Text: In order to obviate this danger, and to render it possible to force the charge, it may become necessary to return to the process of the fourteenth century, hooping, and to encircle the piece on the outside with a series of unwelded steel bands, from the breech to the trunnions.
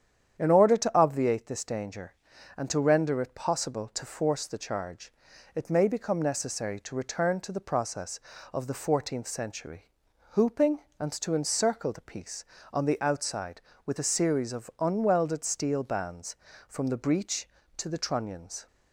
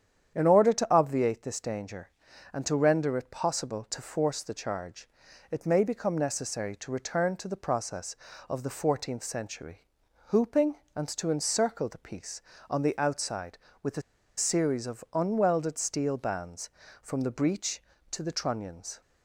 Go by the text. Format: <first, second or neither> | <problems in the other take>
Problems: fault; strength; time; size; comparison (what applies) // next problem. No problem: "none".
first | starts louder than the rest; strong; until 1.4 s; 9 dB; strong in the first // pauses between "a" and "series"; at 14.0 s; 0.36 s long